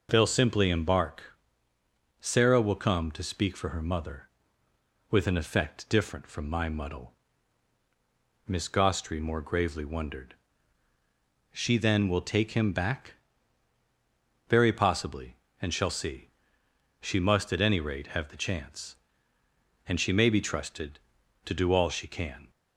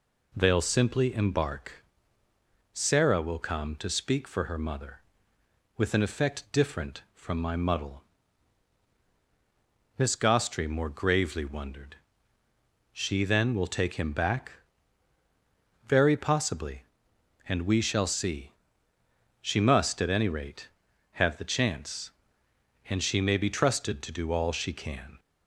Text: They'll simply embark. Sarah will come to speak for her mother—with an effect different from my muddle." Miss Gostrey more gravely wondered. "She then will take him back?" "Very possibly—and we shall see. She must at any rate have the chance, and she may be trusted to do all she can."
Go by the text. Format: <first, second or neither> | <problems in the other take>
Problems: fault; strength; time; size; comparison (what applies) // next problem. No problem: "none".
second | skips "we"; at 15.7 s